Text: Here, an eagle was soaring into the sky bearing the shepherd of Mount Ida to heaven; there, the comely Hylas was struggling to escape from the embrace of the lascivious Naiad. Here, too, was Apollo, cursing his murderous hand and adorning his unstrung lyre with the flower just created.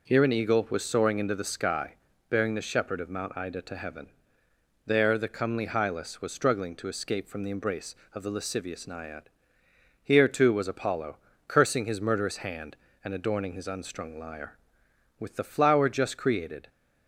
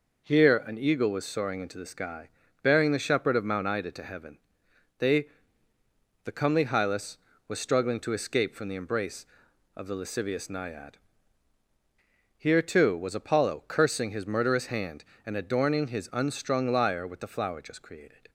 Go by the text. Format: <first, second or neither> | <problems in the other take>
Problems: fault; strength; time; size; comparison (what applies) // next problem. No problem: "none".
first | pauses between "sky" and "bearing"; slight; at 2.2 s; 0.34 s long; slight in the first // says "they" for "there"; at 4.9 s